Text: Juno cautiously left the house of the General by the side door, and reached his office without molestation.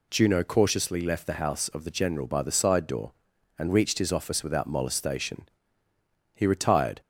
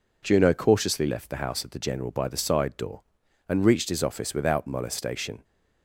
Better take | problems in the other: second | goes on to say "He retired"; noticeable; from 6.3 s on; 0.66 s long

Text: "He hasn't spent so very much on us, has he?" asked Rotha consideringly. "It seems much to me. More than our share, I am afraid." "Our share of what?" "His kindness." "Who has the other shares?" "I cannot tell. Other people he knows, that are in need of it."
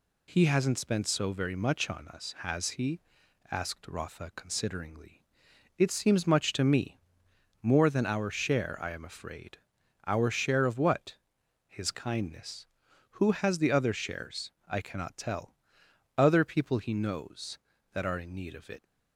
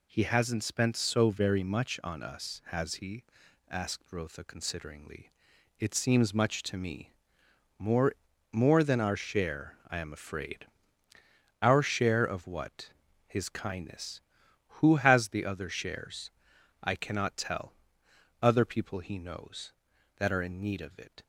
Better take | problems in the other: first | says "More" twice; at 8.5 s

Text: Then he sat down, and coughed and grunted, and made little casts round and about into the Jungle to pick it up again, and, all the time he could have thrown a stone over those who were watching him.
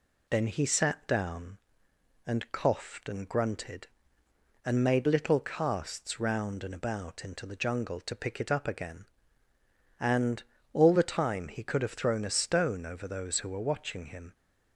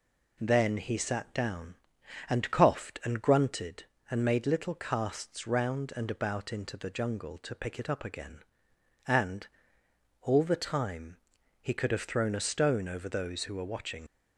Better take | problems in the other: first | pauses between "time" and "he"; noticeable; at 11.1 s; 0.46 s long // stops before "him"; at 14.0 s

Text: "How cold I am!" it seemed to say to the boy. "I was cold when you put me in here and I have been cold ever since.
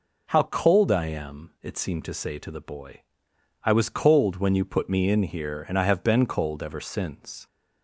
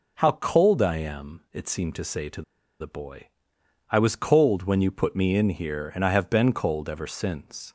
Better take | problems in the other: first | pauses between "to" and "the"; at 2.4 s; 0.37 s long

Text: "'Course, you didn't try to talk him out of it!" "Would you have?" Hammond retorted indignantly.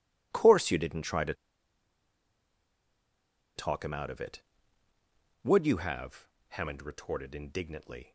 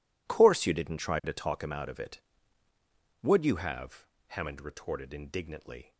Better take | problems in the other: second | pauses between "to" and "talk"; strong; at 1.3 s; 2.2 s long

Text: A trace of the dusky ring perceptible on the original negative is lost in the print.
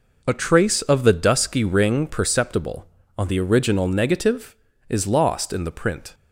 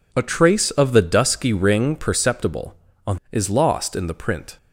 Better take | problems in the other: first | skips "the original negative"; at 3.2 s

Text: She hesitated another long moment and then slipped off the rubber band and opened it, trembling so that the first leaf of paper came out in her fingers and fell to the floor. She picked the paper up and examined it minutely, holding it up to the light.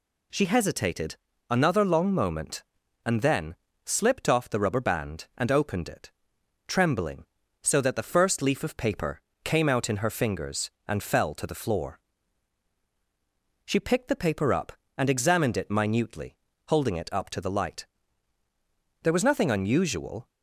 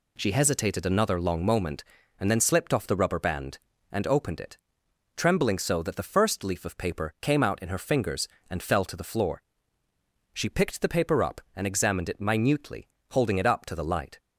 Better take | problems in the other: second | pauses between "hesitated" and "another"; slight; at 1.1 s; 0.32 s long // pauses between "then" and "slipped"; slight; at 3.5 s; 0.30 s long // pauses between "paper" and "came"; slight; at 9.1 s; 0.24 s long // goes on to say "There was nothing unusual"; noticeable; from 19.0 s on; 1.2 s long

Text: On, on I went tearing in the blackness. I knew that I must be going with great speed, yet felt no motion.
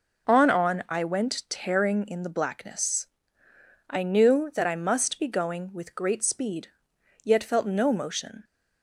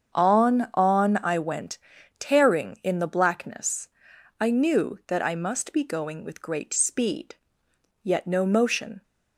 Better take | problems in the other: first | starts louder than the rest; strong; until 1.1 s; 7 dB // pauses between "went" and "tearing"; at 1.7 s; 0.40 s long // skips "felt"; at 8.2 s

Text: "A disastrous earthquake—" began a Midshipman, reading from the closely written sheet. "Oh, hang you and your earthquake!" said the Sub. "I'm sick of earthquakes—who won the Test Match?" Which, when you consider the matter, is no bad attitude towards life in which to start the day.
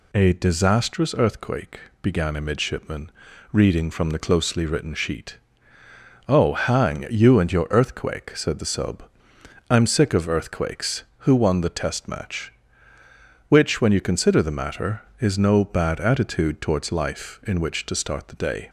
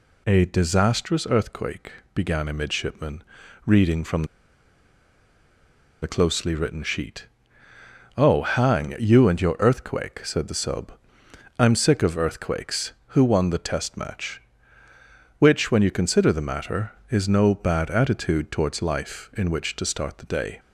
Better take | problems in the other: first | pauses between "from" and "the"; strong; at 4.2 s; 1.7 s long

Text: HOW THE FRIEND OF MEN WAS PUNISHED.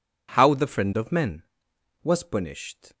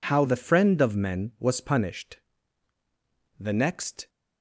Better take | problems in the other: first | goes on to say "The next"; noticeable; from 3.3 s on; 0.70 s long

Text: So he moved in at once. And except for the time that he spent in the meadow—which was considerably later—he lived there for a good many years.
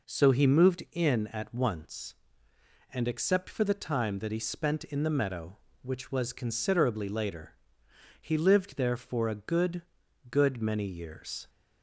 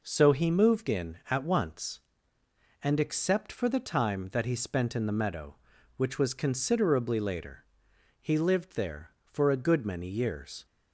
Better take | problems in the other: second | says "good" twice; at 10.2 s

